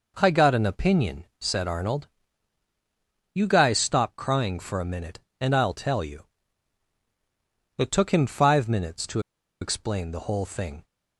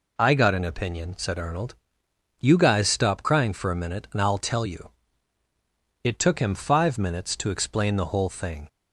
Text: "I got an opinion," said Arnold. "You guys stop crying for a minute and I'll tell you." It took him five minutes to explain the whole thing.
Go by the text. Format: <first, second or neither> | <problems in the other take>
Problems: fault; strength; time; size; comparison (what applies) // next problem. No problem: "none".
second | pauses between "to" and "explain"; at 9.1 s; 0.42 s long